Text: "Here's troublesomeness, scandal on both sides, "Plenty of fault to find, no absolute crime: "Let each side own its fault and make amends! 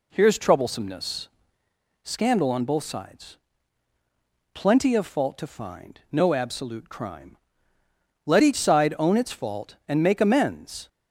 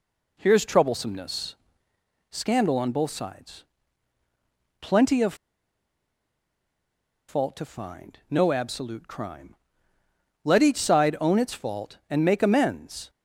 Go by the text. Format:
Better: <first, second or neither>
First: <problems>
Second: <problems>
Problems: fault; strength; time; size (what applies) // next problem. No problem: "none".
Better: first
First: none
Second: pauses between "of" and "fault"; strong; at 5.3 s; 1.9 s long